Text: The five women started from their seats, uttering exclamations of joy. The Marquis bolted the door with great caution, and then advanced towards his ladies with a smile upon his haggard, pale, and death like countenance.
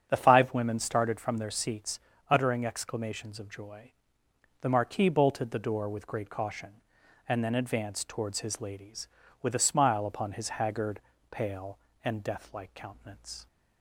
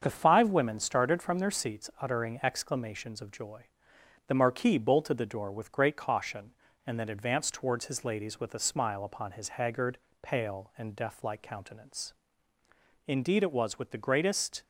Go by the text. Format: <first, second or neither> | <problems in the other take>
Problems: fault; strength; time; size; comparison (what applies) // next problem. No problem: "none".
first | starts louder than the rest; until 1.0 s; 7 dB; strong in the first // goes on to say "Indeed it was with the greatest"; from 13.0 s on; 1.5 s long